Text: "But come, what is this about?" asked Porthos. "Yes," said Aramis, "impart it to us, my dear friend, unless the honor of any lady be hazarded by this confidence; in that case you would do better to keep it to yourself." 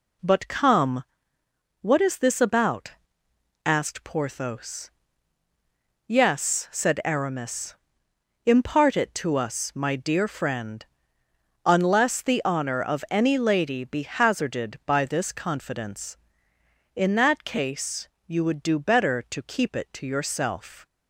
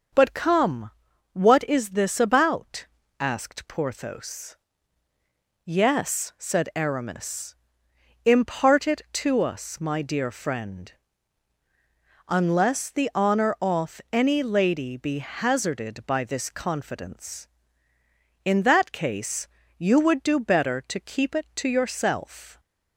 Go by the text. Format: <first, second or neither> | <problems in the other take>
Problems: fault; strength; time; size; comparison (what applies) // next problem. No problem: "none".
first | starts louder than the rest; until 1.5 s; 6.5 dB // says "off" for "of"; at 13.5 s // pauses between "case" and "you"; slight; at 19.4 s; 0.30 s long; slight in the first